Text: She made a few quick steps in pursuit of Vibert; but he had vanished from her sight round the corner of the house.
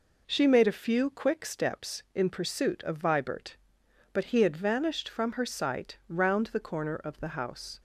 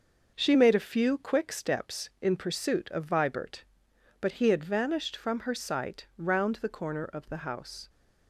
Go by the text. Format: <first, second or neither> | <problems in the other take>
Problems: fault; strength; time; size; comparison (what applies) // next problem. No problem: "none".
first | gets quieter; strong; throughout; 7.5 dB